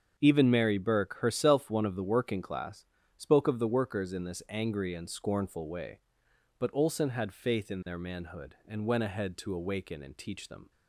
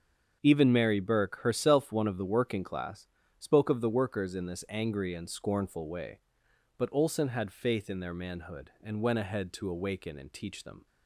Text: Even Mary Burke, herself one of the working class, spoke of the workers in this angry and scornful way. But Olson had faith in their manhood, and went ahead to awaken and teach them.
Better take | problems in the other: neither | starts louder than the rest; the same in both

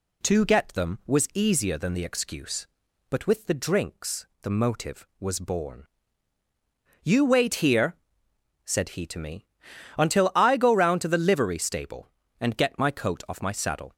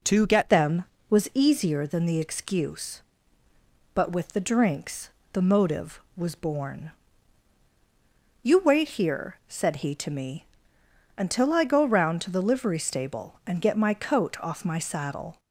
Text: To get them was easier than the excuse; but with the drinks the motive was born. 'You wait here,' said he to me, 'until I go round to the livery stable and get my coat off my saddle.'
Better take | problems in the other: first | changes voice at "them"; from 0.4 s on; 14.9 s long // pauses between "drinks" and "the"; slight; at 5.0 s; 0.24 s long; slight in the first

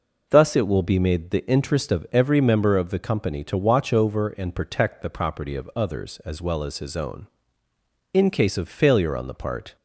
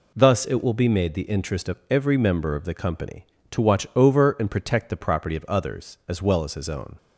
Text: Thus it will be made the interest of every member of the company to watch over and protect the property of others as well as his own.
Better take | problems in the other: second | goes on to say "In case of failure on the part"; from 8.1 s on; 1.6 s long

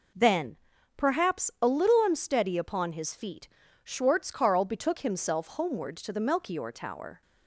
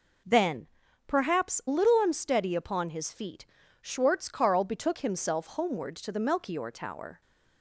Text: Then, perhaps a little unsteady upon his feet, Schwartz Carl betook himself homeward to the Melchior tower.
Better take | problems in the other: first | skips "a"; at 1.6 s

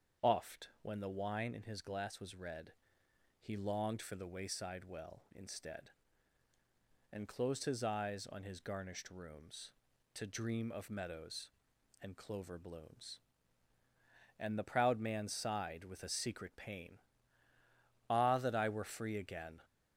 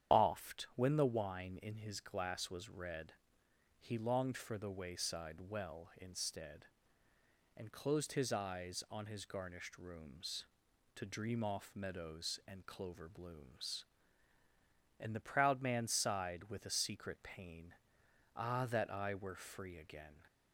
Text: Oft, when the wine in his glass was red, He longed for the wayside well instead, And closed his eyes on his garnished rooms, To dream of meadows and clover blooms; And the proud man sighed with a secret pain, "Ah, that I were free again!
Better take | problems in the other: first | starts louder than the rest; strong; until 1.2 s; 8.5 dB; strong in the first // says "off" for "of"; at 11.4 s

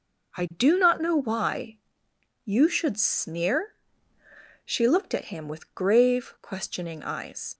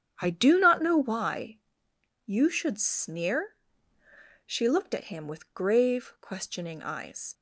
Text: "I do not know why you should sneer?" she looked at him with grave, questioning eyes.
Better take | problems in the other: first | starts louder than the rest; strong; until 1.2 s; 9 dB // pauses between "why" and "you"; noticeable; at 1.5 s; 0.66 s long; noticeable in the first

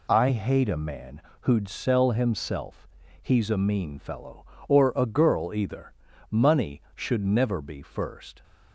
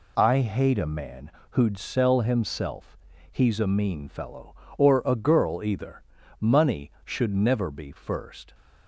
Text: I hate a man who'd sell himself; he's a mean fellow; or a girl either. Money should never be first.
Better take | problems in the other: neither | pauses between "man" and "who'd"; slight; the same in both

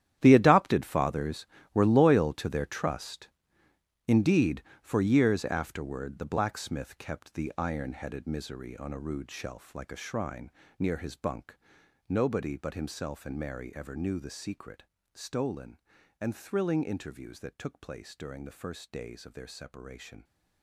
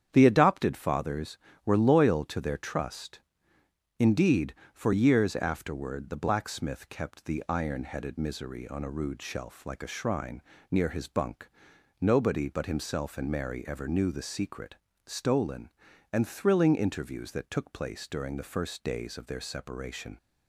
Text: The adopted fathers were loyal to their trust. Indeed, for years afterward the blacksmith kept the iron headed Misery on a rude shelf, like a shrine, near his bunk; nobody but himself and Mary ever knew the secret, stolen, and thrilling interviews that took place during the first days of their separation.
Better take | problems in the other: second | gets quieter; strong; throughout; 15 dB // starts louder than the rest; strong; until 1.2 s; 11 dB; strong in the second

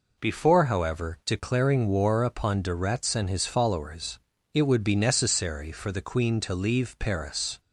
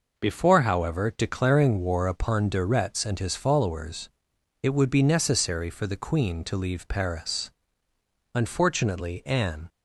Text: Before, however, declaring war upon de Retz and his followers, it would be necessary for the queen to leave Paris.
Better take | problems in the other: first | goes on to say "Unfortunately Anne"; from 8.3 s on; 1.3 s long

